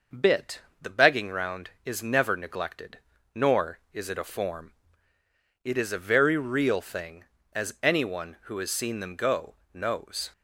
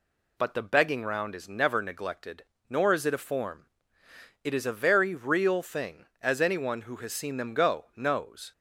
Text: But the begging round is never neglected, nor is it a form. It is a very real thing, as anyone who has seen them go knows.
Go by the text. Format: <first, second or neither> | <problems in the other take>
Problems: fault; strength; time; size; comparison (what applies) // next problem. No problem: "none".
second | says "Bit" for "But"; at 0.1 s // pauses between "go" and "knows"; slight; at 9.5 s; 0.18 s long